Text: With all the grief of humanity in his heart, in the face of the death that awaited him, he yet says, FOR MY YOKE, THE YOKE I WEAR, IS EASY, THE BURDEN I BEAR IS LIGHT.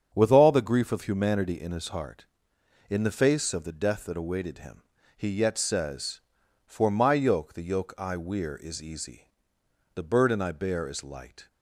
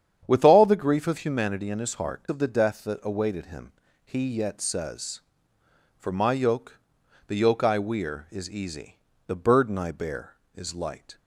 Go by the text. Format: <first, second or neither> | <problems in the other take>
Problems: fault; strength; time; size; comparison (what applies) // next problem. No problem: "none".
first | starts louder than the rest; strong; until 1.2 s; 9 dB; strong in the first // skips "in the face"; at 2.2 s